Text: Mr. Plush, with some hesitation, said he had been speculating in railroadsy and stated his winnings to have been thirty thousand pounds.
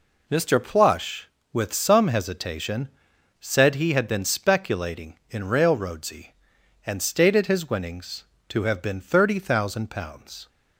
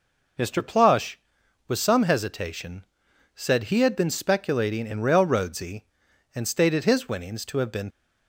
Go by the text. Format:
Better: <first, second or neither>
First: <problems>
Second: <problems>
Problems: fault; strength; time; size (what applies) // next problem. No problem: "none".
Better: first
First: none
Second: stops before "thirty thousand pounds"; at 7.9 s